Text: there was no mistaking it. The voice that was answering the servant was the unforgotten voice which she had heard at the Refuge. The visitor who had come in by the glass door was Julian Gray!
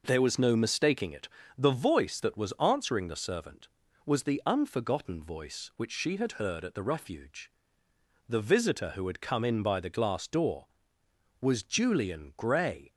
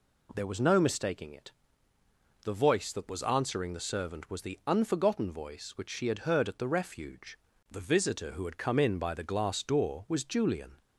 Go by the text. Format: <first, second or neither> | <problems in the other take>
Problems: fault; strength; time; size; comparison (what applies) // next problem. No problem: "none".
first | stops before "Gray"; at 10.8 s